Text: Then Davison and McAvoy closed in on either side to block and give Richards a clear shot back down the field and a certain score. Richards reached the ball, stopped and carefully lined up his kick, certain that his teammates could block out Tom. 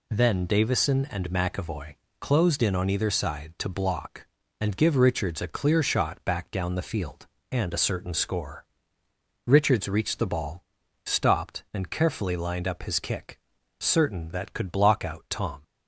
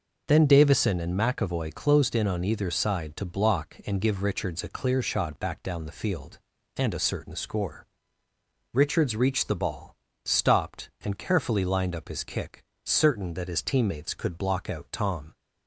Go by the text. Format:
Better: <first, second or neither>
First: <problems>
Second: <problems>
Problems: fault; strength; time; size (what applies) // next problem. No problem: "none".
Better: second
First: pauses between "McAvoy" and "closed"; slight; at 1.9 s; 0.24 s long // skips "his teammates"; at 14.5 s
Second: none